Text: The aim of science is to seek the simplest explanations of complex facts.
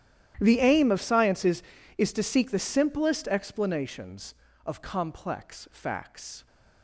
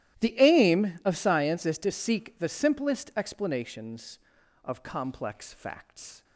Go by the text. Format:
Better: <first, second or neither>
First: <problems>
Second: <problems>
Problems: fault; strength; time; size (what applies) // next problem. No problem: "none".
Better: second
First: starts louder than the rest; strong; until 1.4 s; 12 dB // says "is" twice; at 1.9 s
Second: starts louder than the rest; strong; until 1.2 s; 13 dB